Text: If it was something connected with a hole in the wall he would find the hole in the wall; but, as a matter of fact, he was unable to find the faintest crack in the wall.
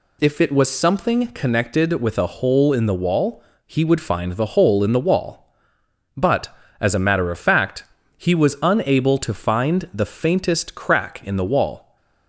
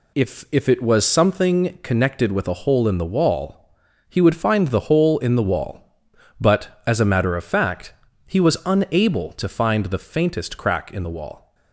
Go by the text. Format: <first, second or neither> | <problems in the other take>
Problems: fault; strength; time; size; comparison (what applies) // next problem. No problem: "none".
first | says "If" twice; at 0.5 s // pauses between "wall" and "he"; noticeable; at 3.5 s; 0.52 s long; slight in the first